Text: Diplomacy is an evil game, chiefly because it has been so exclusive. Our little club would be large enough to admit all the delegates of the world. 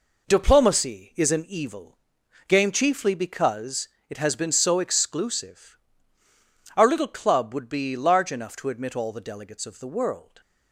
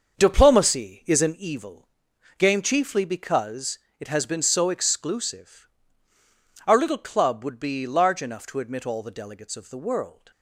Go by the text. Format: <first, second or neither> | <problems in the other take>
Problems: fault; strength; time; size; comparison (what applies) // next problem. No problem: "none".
first | starts louder than the rest; until 1.5 s; 6.5 dB // pauses between "evil" and "game"; noticeable; at 1.8 s; 0.50 s long; noticeable in the first // pauses between "because" and "it"; slight; at 3.7 s; 0.20 s long; slight in the first